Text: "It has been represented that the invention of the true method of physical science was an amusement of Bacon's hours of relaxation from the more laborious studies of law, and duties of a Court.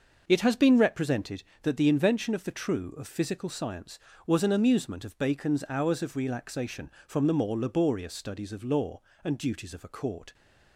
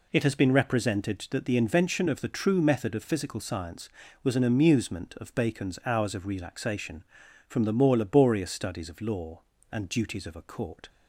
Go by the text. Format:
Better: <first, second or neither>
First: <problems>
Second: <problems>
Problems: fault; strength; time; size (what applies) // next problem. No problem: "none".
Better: second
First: starts louder than the rest; noticeable; until 1.2 s; 6 dB // skips "method"; at 2.9 s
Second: none